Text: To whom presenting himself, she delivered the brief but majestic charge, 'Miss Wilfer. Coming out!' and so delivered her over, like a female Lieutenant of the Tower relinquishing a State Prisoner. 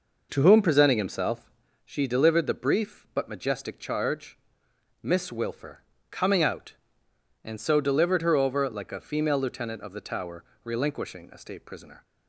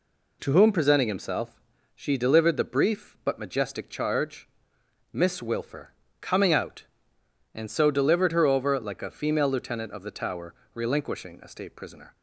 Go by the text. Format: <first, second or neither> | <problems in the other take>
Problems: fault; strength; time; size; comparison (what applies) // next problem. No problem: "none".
second | starts louder than the rest; noticeable; until 1.6 s; 5.5 dB // pauses between "Tower" and "relinquishing"; slight; at 10.4 s; 0.20 s long; slight in the second